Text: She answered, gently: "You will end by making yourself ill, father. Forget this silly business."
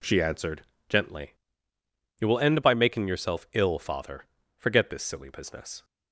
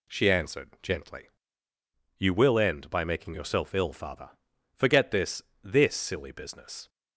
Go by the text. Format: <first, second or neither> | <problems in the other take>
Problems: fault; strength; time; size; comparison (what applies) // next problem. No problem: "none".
first | says "this" twice; at 5.6 s